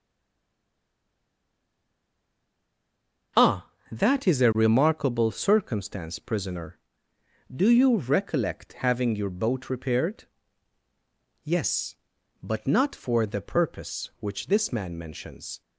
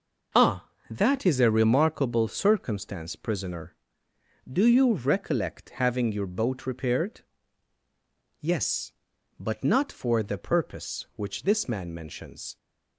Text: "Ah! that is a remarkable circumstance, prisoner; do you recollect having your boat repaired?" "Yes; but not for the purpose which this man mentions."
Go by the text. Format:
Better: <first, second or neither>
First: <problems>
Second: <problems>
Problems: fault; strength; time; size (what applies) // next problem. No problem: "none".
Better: second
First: stays silent before the first word; strong; until 3.3 s; 3.3 s long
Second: none